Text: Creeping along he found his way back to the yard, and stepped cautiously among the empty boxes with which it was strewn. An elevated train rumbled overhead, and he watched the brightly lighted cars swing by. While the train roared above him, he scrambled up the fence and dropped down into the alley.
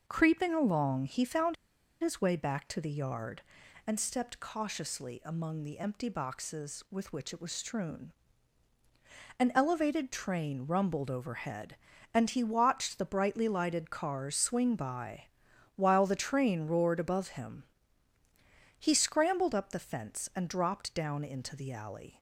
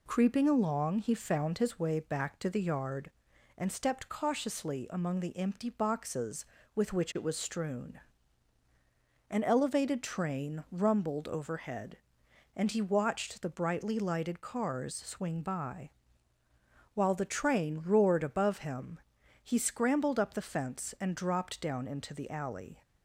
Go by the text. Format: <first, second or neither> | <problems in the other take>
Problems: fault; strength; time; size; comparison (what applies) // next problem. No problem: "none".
second | pauses between "found" and "his"; noticeable; at 1.5 s; 0.46 s long